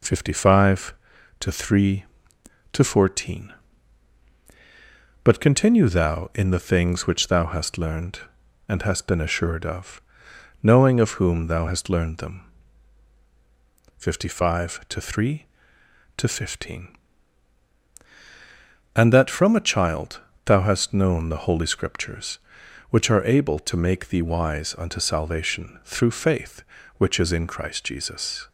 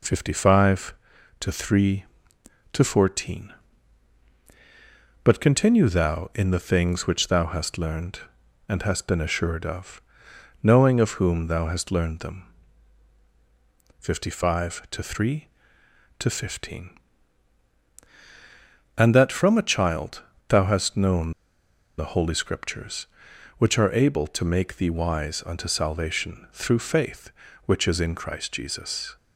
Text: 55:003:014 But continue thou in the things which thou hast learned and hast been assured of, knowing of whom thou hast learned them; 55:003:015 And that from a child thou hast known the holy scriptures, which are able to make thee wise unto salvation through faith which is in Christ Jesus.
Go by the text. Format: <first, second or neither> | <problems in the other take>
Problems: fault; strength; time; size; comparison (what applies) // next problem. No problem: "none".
first | pauses between "child" and "thou"; slight; at 20.2 s; 0.28 s long; slight in the first // pauses between "known" and "the"; noticeable; at 21.3 s; 0.66 s long